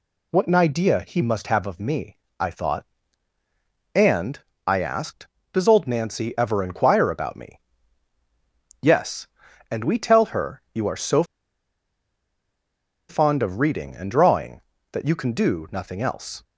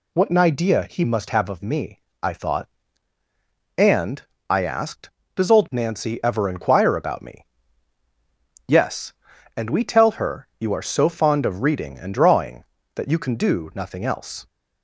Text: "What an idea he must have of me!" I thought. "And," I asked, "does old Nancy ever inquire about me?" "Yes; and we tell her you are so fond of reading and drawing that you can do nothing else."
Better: second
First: pauses between "so" and "fond"; strong; at 11.2 s; 1.8 s long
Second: none

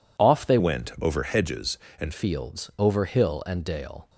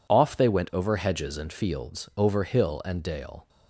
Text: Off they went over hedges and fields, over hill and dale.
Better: second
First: changes voice from "went" to "and"; from 0.5 to 2.1 s; 1.6 s long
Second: none

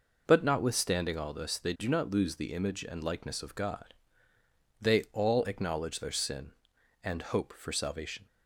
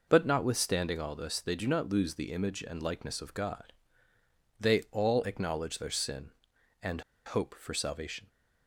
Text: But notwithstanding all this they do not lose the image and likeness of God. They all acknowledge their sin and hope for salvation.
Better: first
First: none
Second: pauses between "and" and "hope"; slight; at 7.0 s; 0.24 s long

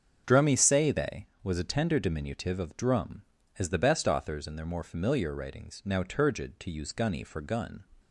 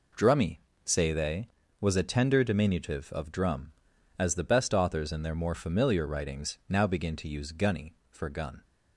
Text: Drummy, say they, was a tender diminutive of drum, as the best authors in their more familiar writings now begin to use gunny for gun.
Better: second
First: starts louder than the rest; until 1.2 s; 6.5 dB // says "turgid" for "begin"; at 6.0 s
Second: none

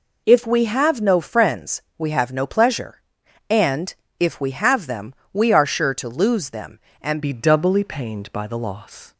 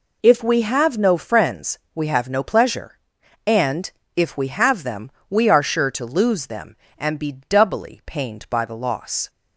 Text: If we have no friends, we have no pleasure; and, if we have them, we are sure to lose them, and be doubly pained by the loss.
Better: second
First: changes voice at "be"; from 7.2 s on; 1.9 s long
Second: none

